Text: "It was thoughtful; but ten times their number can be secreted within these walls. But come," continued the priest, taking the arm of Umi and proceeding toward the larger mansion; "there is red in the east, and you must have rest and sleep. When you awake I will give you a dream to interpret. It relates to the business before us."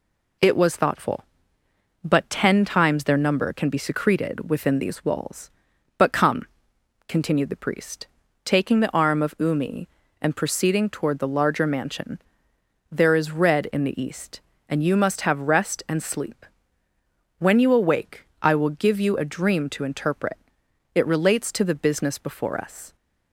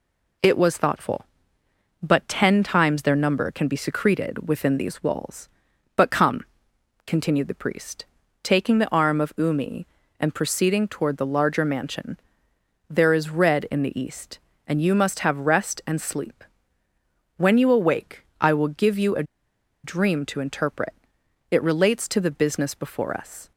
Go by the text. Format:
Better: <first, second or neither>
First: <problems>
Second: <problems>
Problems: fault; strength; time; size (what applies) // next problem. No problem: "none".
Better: first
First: pauses between "awake" and "I"; slight; at 18.2 s; 0.16 s long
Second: pauses between "awake" and "I"; slight; at 18.2 s; 0.16 s long // pauses between "a" and "dream"; noticeable; at 19.2 s; 0.60 s long